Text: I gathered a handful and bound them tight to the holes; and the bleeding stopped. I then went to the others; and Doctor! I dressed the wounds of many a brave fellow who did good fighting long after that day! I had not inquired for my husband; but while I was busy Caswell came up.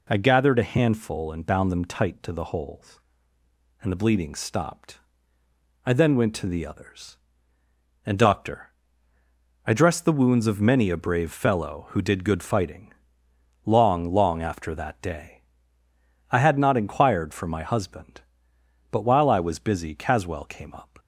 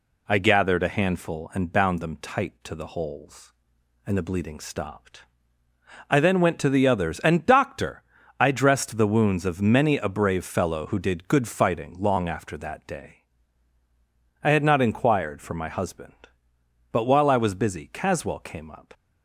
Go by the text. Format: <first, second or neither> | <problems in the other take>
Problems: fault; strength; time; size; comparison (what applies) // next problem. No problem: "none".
second | pauses between "fighting" and "long"; noticeable; at 12.9 s; 0.72 s long // says "long" twice; at 14.1 s